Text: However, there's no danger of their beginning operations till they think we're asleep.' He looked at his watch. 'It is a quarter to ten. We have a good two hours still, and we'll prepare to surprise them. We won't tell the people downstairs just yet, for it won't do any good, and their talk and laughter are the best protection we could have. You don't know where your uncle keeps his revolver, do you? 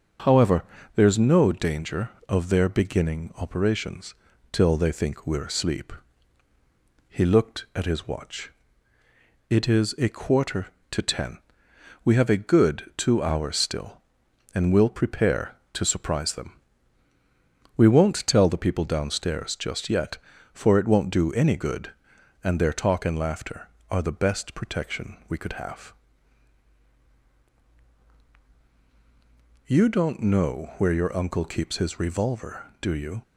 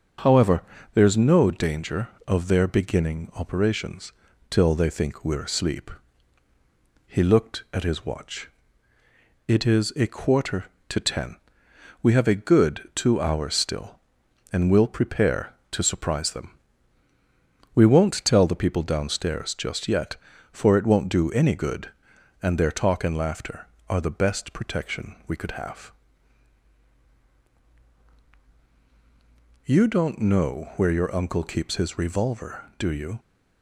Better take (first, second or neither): neither